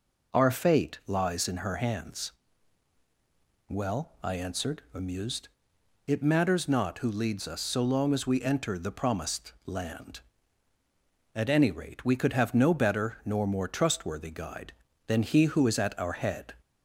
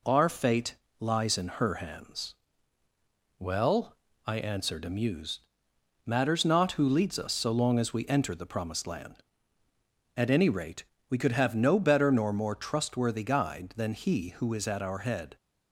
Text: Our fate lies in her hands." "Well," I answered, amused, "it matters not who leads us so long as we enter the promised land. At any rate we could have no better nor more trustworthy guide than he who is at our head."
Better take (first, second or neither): first